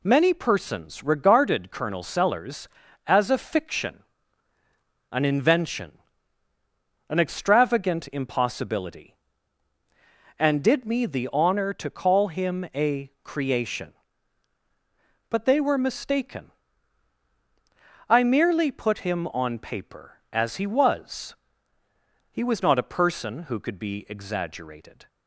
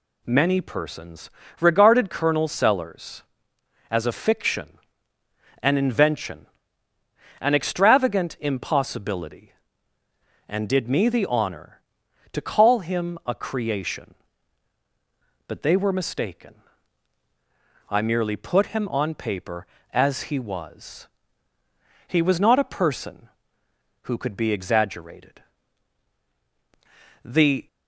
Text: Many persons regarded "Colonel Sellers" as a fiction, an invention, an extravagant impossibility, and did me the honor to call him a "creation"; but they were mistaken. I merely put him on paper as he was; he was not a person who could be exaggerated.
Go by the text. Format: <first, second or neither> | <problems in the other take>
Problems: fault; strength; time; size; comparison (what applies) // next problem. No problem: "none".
first | pauses between "persons" and "regarded"; slight; at 1.2 s; 0.30 s long // goes on to say "The"; slight; from 27.2 s on; 0.42 s long